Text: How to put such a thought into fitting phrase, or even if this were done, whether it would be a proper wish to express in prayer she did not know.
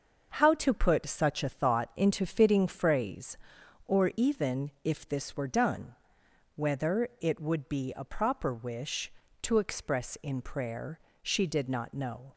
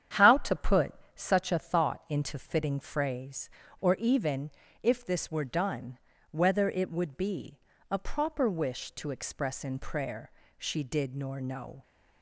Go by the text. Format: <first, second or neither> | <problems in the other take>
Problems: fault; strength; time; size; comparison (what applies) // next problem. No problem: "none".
first | starts louder than the rest; strong; until 1.4 s; 9 dB; noticeable in the first // pauses between "put" and "such"; slight; at 0.9 s; 0.24 s long // pauses between "even" and "if"; slight; at 4.5 s; 0.28 s long // pauses between "be" and "a"; slight; at 7.5 s; 0.32 s long // pauses between "prayer" and "she"; slight; at 10.2 s; 0.26 s long; slight in the first // says "nor" for "not"; at 11.1 s